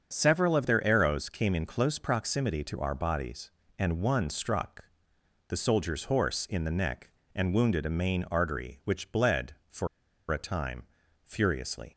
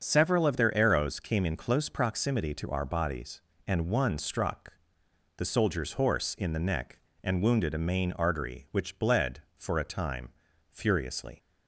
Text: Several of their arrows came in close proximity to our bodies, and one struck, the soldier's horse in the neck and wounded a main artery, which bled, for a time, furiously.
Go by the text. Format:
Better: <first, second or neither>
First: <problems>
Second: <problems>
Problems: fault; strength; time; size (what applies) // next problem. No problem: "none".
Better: second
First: starts louder than the rest; until 1.1 s; 6.5 dB // pauses between "for" and "a"; at 9.8 s; 0.43 s long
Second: starts louder than the rest; until 1.0 s; 6.5 dB